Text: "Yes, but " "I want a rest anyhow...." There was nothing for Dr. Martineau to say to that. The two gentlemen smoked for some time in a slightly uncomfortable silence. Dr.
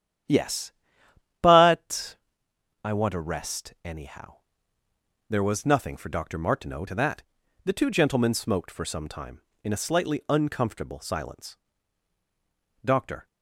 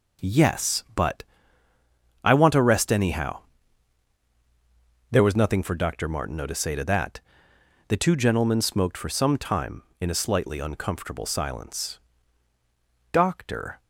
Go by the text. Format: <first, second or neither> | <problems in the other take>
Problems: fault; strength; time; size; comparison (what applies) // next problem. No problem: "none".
second | starts louder than the rest; strong; until 1.9 s; 10 dB // skips "to say"; at 6.8 s